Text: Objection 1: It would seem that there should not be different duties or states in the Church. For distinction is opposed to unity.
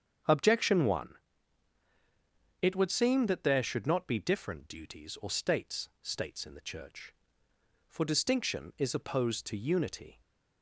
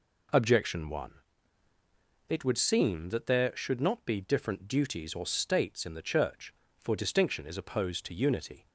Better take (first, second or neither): second